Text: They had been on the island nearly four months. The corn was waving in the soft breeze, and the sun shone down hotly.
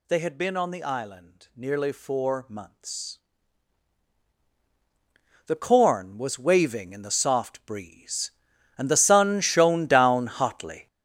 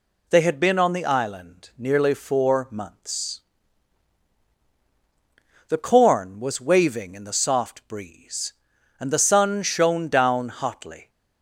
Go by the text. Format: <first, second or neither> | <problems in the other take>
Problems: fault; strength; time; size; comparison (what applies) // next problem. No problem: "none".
second | gets louder; strong; throughout; 9.5 dB